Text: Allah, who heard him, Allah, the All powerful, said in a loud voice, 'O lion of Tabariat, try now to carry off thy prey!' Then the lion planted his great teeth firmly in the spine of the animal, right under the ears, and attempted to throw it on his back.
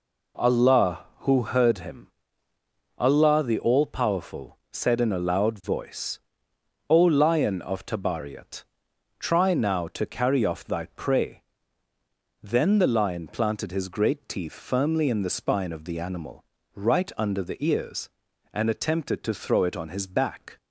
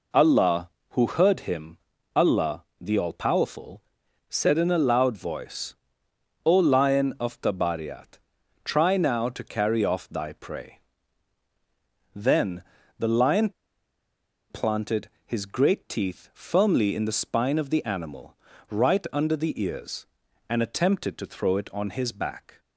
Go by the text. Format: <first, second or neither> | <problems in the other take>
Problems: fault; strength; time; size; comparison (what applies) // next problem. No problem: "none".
first | pauses between "Then" and "the"; at 12.6 s; 0.38 s long // pauses between "lion" and "planted"; at 13.5 s; 0.99 s long // pauses between "planted" and "his"; slight; at 15.0 s; 0.16 s long